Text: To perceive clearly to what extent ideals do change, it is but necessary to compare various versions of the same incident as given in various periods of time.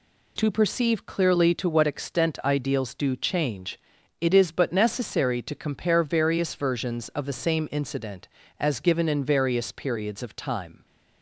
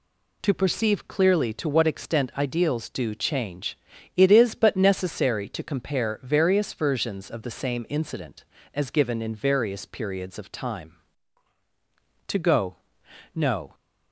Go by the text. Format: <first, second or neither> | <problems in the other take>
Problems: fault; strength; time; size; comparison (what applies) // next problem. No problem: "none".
first | goes on to say "To go no"; from 12.2 s on; 1.4 s long